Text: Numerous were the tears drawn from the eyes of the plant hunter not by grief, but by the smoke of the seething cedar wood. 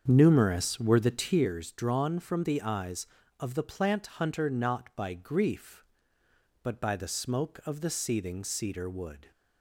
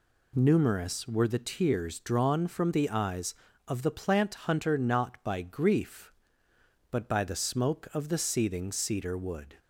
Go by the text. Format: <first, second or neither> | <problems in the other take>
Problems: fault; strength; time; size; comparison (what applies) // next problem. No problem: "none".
second | starts louder than the rest; strong; until 1.5 s; 7 dB